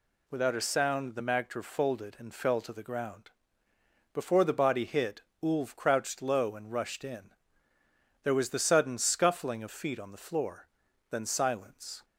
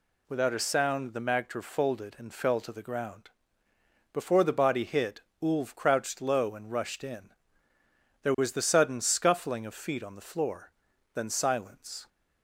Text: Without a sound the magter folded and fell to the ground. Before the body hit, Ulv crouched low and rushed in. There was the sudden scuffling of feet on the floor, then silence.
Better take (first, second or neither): neither